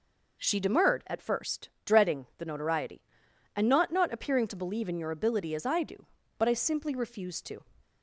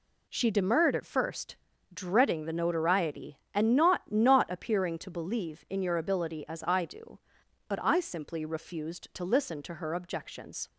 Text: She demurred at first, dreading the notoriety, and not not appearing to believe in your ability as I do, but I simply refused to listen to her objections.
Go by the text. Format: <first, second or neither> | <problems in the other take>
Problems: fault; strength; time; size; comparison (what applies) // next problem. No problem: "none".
second | stops before "listen to her objections"; at 7.8 s